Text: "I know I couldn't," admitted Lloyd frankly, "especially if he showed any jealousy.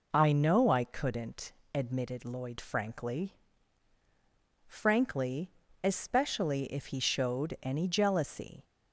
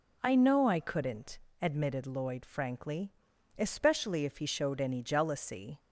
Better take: second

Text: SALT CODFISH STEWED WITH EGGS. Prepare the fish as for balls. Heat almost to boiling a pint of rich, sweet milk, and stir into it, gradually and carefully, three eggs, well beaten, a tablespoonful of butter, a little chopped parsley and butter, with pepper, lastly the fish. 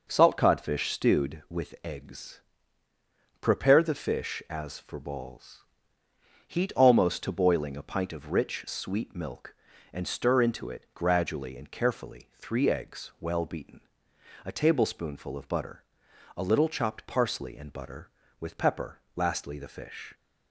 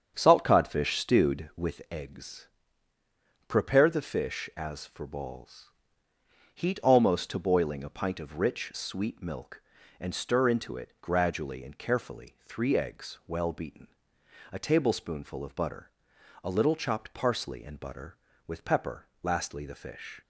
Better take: first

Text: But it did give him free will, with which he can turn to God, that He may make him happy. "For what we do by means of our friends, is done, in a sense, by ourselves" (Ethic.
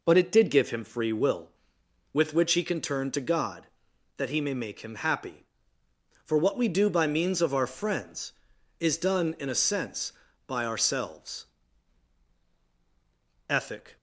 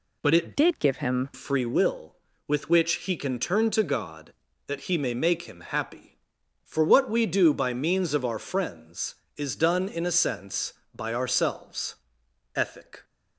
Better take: first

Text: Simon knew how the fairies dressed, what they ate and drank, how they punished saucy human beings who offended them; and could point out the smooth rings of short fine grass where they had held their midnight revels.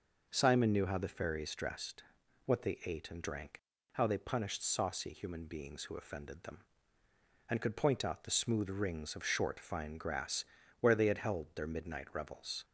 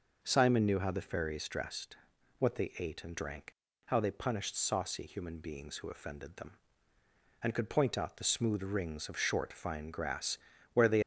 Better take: first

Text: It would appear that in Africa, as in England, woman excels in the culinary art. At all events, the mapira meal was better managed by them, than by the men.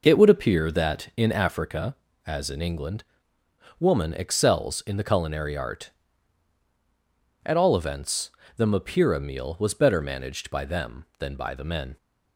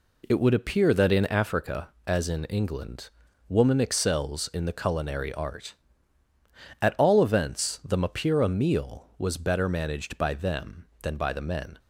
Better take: neither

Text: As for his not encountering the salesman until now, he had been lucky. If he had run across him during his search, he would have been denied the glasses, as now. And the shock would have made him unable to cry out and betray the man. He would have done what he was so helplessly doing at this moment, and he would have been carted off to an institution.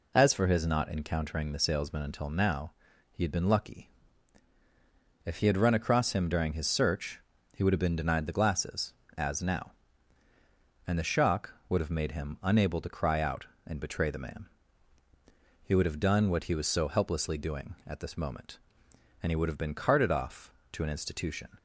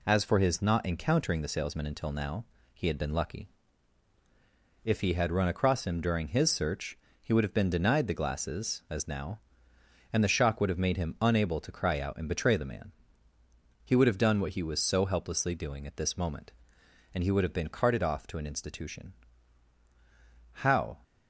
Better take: first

